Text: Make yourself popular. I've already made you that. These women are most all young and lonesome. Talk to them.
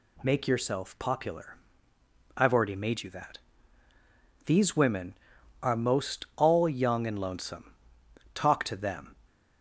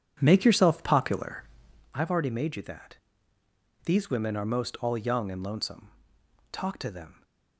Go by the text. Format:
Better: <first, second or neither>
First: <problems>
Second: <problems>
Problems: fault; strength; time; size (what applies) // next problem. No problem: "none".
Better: first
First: none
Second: starts louder than the rest; strong; until 2.0 s; 8.5 dB